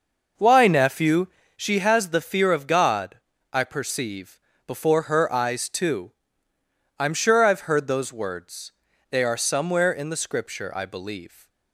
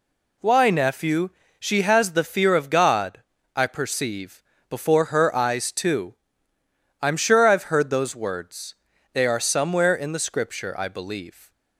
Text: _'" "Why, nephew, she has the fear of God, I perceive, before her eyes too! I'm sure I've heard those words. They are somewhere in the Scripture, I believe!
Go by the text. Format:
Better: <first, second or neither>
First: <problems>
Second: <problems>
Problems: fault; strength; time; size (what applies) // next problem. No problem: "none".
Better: second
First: starts louder than the rest; noticeable; until 1.6 s; 5.5 dB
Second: none